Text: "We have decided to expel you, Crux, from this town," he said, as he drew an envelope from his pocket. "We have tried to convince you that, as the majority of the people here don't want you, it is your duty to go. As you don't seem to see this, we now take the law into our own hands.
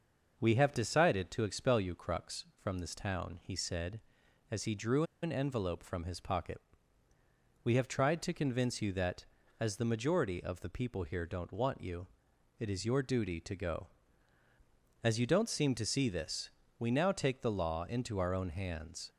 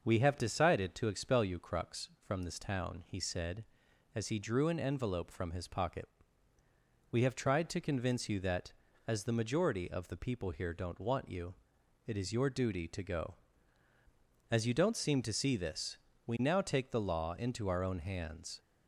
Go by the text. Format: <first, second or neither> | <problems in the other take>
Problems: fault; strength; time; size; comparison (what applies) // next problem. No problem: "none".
second | starts louder than the rest; noticeable; until 1.4 s; 6 dB; noticeable in the second // pauses between "drew" and "an"; slight; at 5.0 s; 0.19 s long